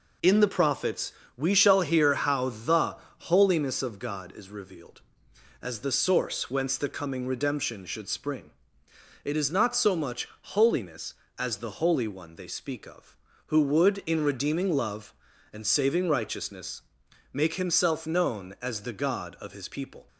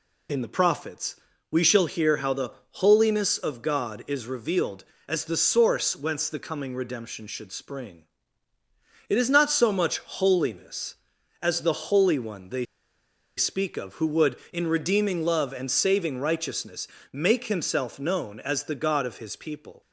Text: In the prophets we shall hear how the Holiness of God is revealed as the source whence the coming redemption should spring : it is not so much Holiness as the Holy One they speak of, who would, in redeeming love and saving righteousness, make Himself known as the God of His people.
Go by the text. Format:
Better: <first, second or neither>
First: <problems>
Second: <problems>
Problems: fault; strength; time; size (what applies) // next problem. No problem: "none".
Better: first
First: pauses between "prophets" and "we"; slight; at 1.1 s; 0.24 s long // pauses between "the" and "Holiness"; slight; at 2.9 s; 0.24 s long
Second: pauses between "prophets" and "we"; slight; at 1.1 s; 0.34 s long // pauses between "the" and "Holiness"; slight; at 2.5 s; 0.22 s long // pauses between "they" and "speak"; noticeable; at 12.6 s; 0.72 s long